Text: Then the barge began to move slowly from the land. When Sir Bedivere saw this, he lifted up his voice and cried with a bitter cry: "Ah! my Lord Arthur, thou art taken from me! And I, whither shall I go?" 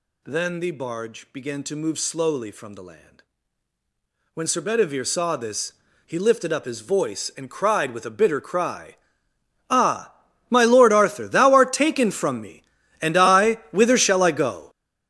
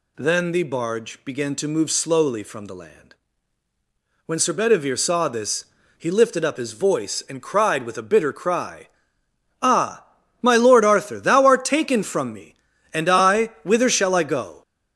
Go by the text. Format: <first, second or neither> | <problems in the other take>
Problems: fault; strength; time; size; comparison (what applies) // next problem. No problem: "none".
second | gets louder; strong; throughout; 13.5 dB